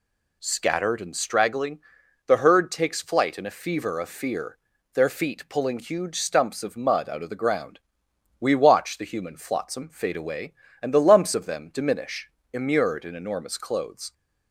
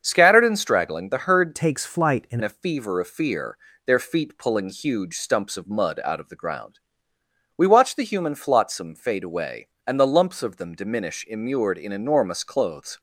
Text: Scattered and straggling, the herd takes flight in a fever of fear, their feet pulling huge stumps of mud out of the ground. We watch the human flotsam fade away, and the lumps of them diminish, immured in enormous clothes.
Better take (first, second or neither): first